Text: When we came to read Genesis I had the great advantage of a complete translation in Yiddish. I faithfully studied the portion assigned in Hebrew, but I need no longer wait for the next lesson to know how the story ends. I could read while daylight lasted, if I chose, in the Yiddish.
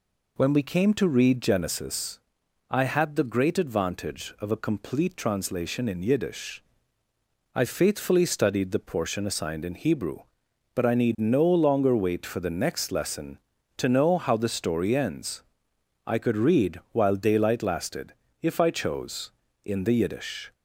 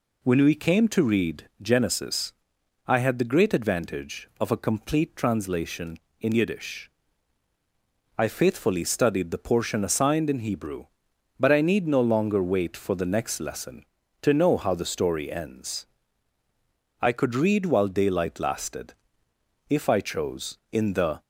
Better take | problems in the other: first | pauses between "Genesis" and "I"; noticeable; at 2.3 s; 0.54 s long; noticeable in the first // stops before "Yiddish"; at 21.2 s

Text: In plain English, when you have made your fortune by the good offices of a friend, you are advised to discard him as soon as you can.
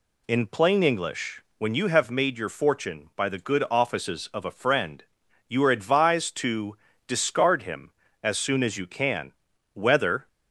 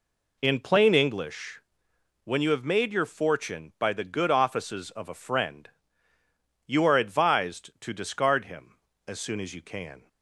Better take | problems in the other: second | pauses between "to" and "discard"; slight; at 6.7 s; 0.30 s long // goes on to say "Whether"; from 9.7 s on; 0.54 s long

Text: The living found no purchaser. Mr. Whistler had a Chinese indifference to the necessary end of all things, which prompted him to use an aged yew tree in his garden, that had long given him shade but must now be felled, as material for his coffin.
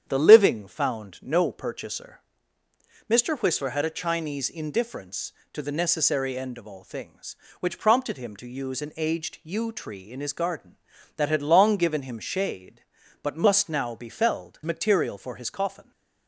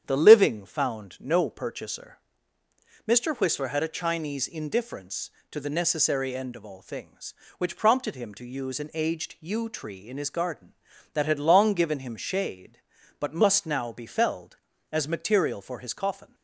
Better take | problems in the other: second | starts louder than the rest; strong; until 1.0 s; 8.5 dB; strong in the second // skips "as"; at 14.6 s

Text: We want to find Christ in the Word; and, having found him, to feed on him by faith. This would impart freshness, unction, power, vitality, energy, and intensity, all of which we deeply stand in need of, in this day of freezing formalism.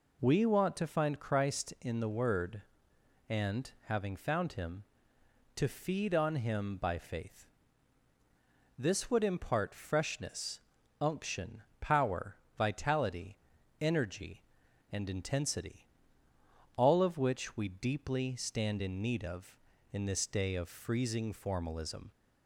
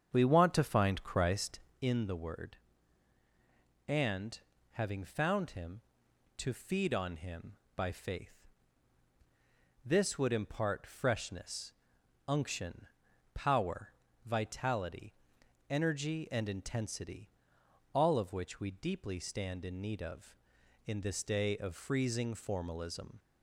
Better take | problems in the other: first | starts louder than the rest; strong; until 1.8 s; 7.5 dB

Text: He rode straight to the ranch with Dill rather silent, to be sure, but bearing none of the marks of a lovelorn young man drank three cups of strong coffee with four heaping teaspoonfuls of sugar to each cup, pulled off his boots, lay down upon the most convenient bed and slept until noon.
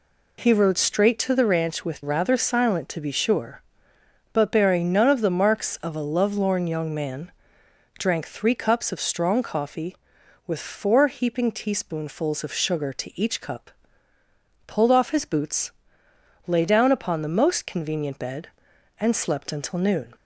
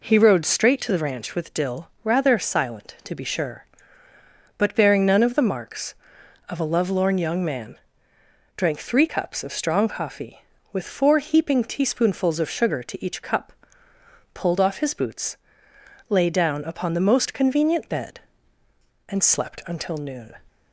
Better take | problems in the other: second | skips "Dill"; at 2.0 s // pauses between "man" and "drank"; noticeable; at 7.2 s; 0.68 s long; noticeable in the second

